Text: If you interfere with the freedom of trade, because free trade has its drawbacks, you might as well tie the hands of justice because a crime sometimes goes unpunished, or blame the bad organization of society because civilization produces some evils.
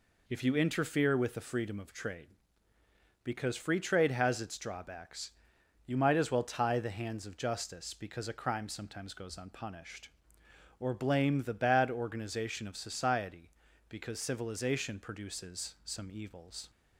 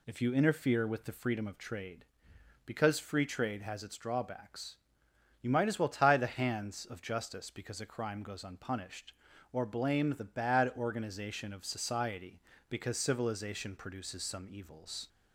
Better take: first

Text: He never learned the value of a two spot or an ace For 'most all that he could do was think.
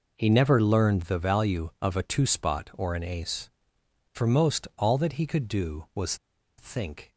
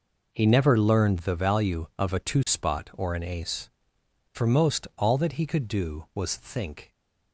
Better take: second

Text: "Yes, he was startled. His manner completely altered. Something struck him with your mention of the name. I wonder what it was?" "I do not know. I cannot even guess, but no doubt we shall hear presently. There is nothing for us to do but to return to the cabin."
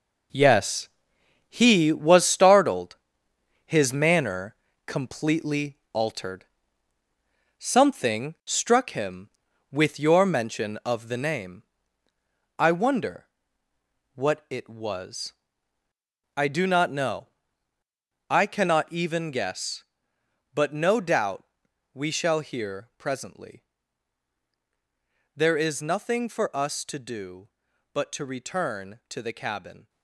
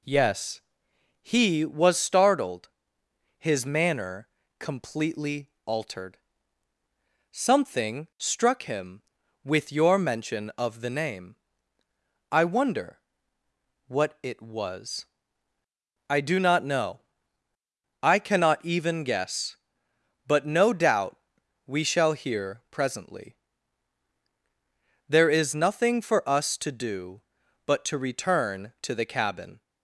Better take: second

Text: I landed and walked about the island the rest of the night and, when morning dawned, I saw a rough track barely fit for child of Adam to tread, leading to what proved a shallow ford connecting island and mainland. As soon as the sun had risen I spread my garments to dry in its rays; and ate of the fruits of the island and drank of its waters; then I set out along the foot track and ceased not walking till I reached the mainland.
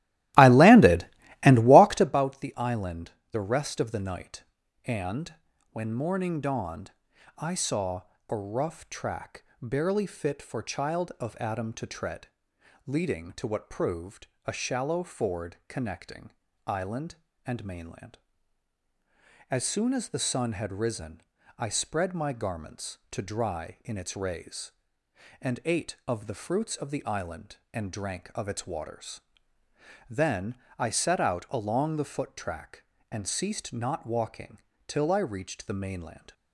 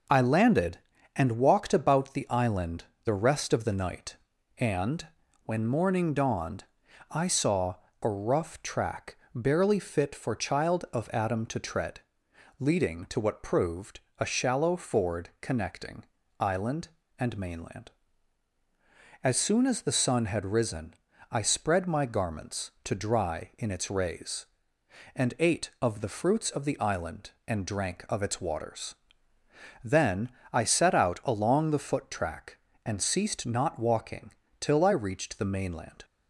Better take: second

